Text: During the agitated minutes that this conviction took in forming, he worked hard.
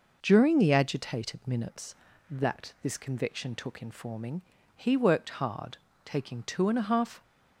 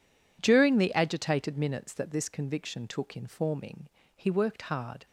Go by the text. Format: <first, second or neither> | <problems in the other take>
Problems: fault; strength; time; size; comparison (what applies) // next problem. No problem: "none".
second | goes on to say "Taking two and a half"; noticeable; from 6.0 s on; 1.1 s long